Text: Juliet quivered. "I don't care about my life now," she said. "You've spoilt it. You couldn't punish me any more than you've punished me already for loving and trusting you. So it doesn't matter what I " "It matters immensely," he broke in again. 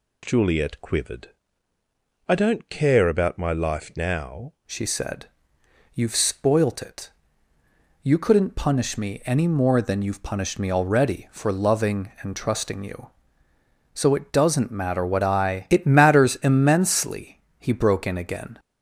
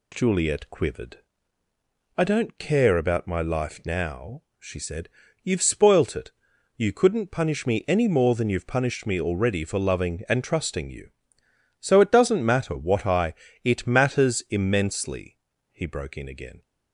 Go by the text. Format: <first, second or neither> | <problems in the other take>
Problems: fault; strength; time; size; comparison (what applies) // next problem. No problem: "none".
second | changes voice at "she"; from 4.6 s on; 13.9 s long